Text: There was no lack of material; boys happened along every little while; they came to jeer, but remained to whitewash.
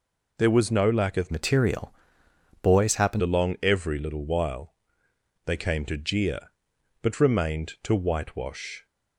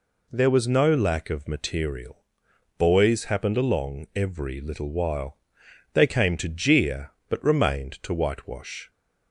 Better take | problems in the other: second | changes voice from "material" to "happened"; from 1.2 to 3.2 s; 2.0 s long

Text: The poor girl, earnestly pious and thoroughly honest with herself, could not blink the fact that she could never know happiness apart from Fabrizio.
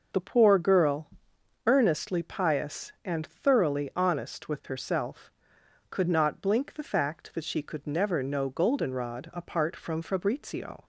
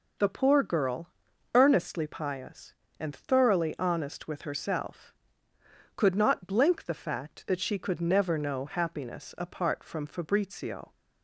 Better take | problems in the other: second | starts louder than the rest; until 1.7 s; 6.5 dB // says "goldenrod" for "happiness"; at 8.5 s

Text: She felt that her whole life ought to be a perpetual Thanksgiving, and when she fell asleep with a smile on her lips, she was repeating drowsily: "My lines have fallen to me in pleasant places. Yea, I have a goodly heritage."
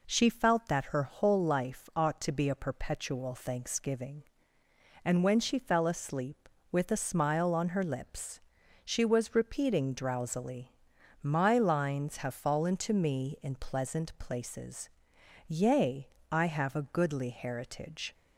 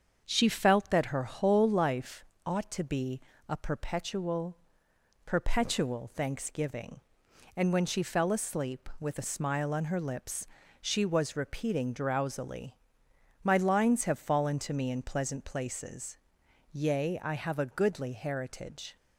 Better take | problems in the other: first | starts louder than the rest; until 1.2 s; 7 dB // pauses between "life" and "ought"; slight; at 2.2 s; 0.22 s long // pauses between "be" and "a"; slight; at 3.1 s; 0.28 s long // says "perpetual" twice; at 5.2 s

